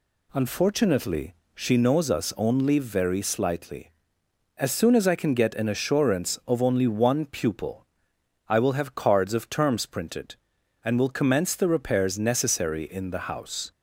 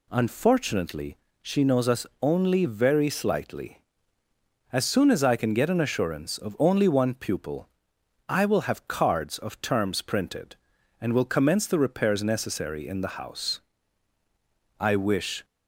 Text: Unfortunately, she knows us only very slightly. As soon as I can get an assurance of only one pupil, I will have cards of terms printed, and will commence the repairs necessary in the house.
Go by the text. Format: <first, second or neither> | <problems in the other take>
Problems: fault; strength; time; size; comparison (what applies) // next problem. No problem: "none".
first | pauses between "us" and "only"; slight; at 2.0 s; 0.16 s long // goes on to say "I wish"; noticeable; from 14.7 s on; 0.66 s long